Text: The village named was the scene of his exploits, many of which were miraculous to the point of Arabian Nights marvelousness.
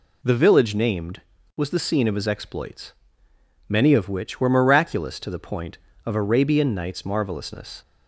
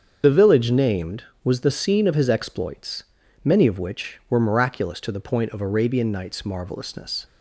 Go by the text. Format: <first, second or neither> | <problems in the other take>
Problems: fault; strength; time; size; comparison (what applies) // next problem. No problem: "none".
first | loses the start of "The"; at 0.2 s; 50 ms // starts louder than the rest; until 1.2 s; 7 dB